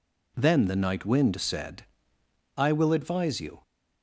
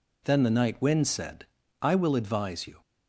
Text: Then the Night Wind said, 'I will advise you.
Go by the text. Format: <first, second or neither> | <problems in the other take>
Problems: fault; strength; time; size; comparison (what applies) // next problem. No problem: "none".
neither | none